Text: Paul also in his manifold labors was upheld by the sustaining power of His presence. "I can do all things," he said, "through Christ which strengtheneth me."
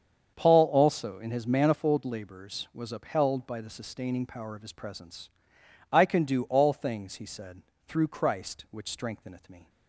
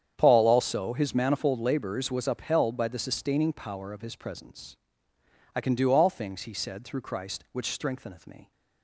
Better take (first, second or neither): first